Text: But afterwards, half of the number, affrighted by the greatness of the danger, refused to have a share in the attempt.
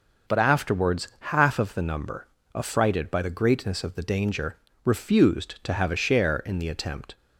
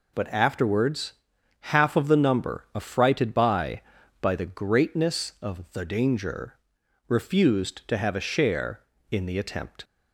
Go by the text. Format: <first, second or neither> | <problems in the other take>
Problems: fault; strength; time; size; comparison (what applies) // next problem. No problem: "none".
first | says "by" twice; at 4.2 s